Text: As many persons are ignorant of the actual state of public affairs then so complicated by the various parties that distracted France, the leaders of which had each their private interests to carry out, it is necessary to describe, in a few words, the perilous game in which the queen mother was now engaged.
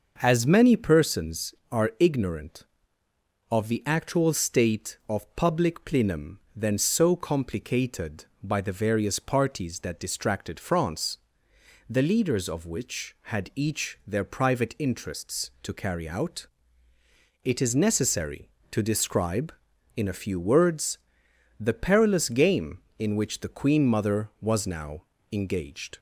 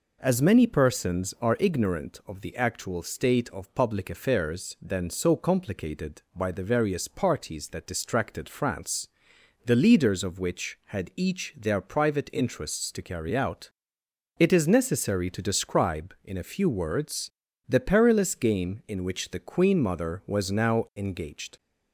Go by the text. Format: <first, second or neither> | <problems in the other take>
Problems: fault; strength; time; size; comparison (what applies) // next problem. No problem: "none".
second | starts louder than the rest; noticeable; until 1.2 s; 6 dB // says "plenum" for "affairs"; at 5.8 s // pauses between "now" and "engaged"; slight; at 25.0 s; 0.28 s long